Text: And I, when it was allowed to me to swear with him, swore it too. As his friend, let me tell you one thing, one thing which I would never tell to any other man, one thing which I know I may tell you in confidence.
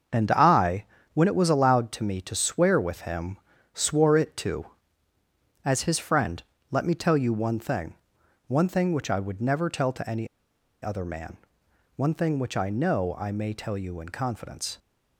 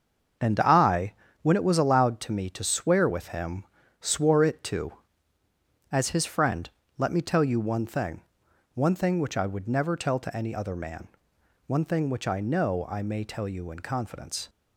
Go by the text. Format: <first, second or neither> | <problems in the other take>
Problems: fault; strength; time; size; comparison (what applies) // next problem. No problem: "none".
second | starts louder than the rest; until 1.4 s; 6.5 dB; also in the second // pauses between "any" and "other"; noticeable; at 10.2 s; 0.54 s long